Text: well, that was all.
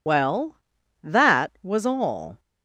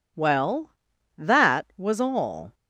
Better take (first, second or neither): second